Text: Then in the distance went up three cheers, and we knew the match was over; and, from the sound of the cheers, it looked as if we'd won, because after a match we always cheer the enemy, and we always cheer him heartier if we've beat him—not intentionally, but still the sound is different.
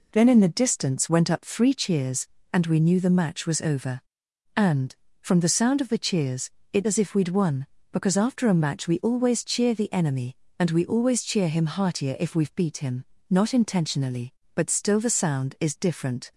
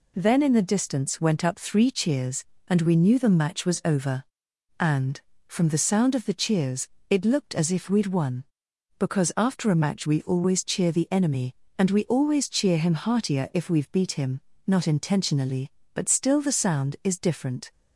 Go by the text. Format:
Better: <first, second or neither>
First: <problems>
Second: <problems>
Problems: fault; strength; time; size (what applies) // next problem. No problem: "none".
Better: second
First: skips "looked"; at 6.8 s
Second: none